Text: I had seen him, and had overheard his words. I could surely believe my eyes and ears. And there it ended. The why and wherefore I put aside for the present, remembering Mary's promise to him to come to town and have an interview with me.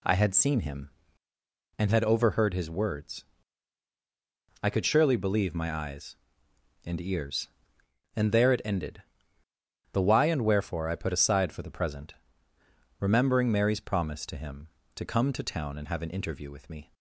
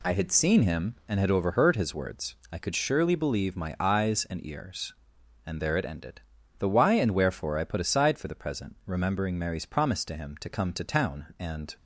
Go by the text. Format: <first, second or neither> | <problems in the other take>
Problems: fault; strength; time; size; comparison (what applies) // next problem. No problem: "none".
first | stops before "have an interview with me"; at 11.7 s